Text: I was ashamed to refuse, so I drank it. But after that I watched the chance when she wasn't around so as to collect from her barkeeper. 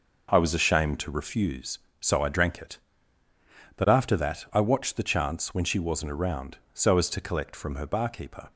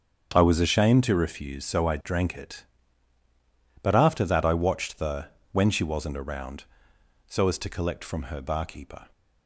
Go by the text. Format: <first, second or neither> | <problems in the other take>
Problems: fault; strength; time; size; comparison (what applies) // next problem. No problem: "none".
first | starts louder than the rest; strong; until 1.3 s; 7.5 dB // skips "chance"; at 5.3 s